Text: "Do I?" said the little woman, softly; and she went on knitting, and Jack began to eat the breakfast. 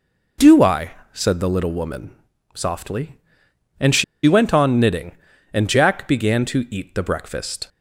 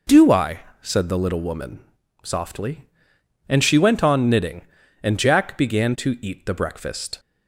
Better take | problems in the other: second | pauses between "she" and "went"; slight; at 4.0 s; 0.22 s long

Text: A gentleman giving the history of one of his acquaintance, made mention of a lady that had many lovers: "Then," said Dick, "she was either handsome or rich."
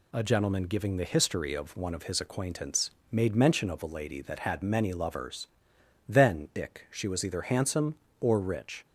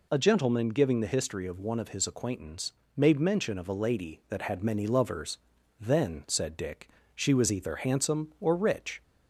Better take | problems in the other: second | skips "said"; at 6.5 s

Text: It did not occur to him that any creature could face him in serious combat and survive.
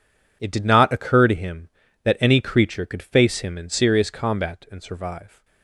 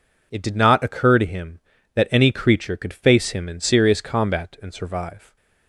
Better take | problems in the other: second | gets quieter; strong; throughout; 13 dB

